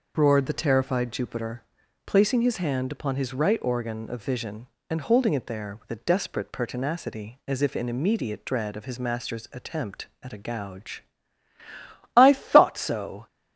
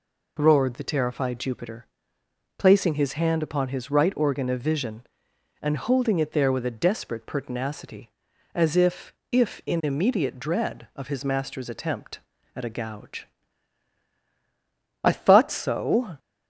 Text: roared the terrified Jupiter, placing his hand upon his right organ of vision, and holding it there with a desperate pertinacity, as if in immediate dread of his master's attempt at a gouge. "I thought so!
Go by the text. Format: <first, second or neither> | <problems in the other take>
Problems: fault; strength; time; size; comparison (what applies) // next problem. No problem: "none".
first | says "if" twice; at 9.3 s